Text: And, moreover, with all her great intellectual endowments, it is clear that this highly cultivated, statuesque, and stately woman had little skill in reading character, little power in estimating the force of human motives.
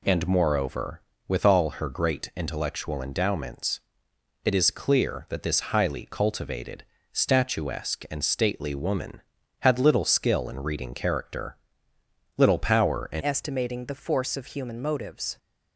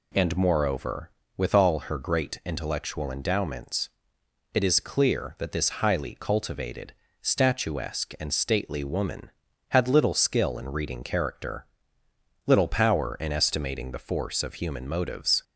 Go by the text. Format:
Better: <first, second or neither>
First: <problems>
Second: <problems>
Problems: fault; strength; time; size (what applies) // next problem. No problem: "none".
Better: second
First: changes voice at "estimating"; from 13.2 s on; 2.1 s long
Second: none